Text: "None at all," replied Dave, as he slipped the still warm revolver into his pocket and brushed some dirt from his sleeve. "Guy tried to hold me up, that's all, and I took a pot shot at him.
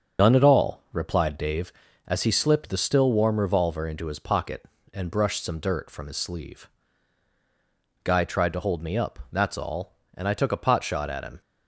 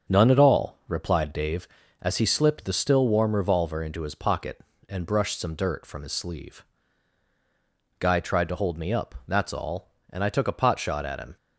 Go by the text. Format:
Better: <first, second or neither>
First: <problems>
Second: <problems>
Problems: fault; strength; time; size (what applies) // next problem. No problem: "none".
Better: second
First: loses the start of "None"; at 0.1 s; 60 ms // starts louder than the rest; strong; until 1.3 s; 7 dB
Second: starts louder than the rest; until 1.1 s; 7 dB